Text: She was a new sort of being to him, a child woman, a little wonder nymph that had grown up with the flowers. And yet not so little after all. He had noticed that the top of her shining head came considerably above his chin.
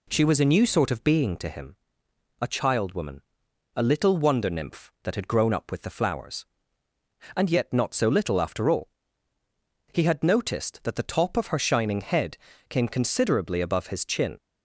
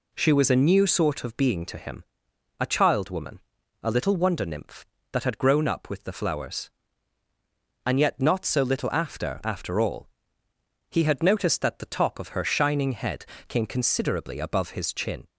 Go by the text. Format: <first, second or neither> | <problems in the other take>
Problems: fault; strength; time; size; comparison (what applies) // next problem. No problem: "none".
first | says "after" twice; at 9.4 s // pauses between "head" and "came"; slight; at 13.2 s; 0.24 s long; slight in the first